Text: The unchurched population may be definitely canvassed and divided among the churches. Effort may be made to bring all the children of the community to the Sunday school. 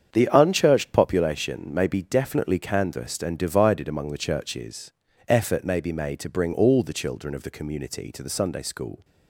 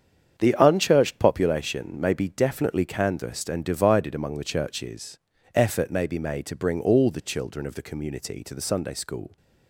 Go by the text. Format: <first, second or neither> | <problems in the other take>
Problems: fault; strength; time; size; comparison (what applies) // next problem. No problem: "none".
neither | starts louder than the rest; strong; the same in both